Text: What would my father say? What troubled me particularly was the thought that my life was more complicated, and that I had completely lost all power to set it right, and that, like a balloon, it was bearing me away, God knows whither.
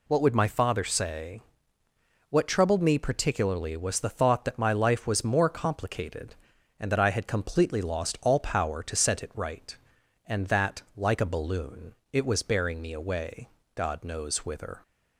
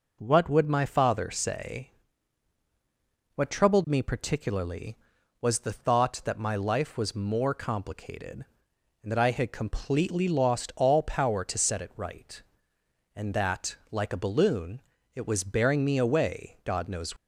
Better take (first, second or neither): first